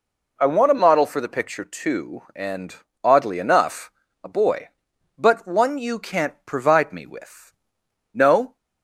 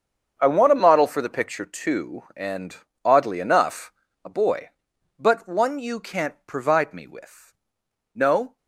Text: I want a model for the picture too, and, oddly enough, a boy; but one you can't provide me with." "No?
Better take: first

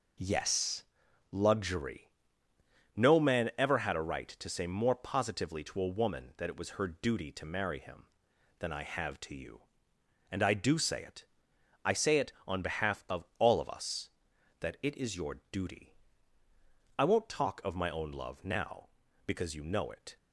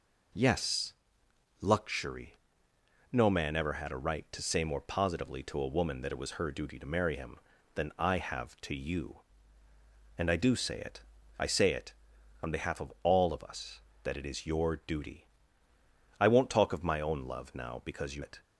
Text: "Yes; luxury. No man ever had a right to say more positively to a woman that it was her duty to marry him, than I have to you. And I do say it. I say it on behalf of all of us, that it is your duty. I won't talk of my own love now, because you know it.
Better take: first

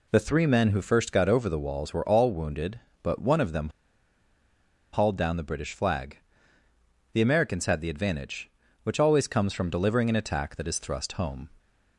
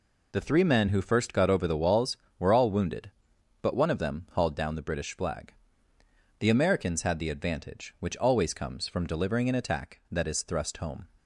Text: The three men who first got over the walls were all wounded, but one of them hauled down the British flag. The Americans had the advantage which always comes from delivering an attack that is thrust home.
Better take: second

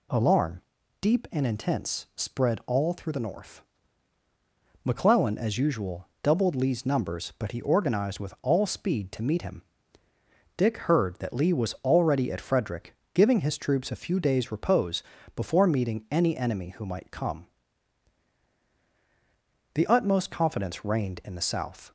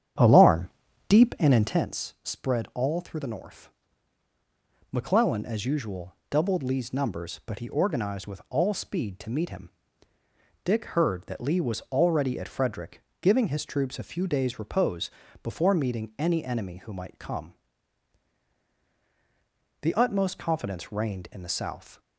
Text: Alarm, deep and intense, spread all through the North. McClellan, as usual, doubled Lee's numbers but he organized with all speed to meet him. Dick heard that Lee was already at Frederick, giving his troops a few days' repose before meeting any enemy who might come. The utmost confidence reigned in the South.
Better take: first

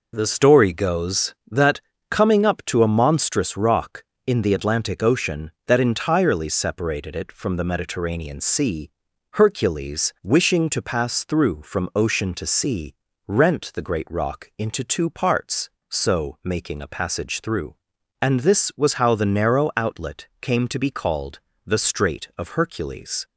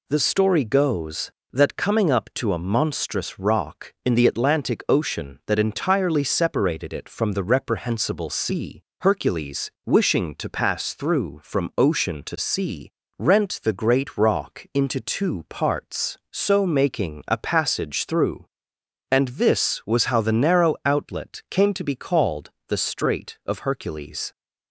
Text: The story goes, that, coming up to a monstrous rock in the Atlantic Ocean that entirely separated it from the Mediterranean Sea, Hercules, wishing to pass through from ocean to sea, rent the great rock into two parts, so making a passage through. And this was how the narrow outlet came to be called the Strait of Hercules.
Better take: first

